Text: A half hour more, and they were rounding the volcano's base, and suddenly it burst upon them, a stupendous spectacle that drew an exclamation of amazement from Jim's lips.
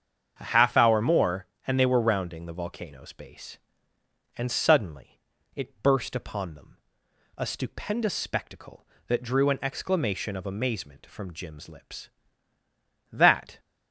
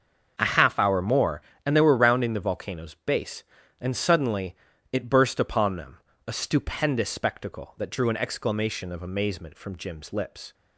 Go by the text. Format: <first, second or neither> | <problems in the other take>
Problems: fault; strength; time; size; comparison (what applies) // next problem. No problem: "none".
second | starts louder than the rest; strong; until 1.4 s; 7.5 dB; also in the second // pauses between "suddenly" and "it"; slight; at 5.1 s; 0.36 s long; slight in the second // goes on to say "That"; slight; from 13.1 s on; 0.48 s long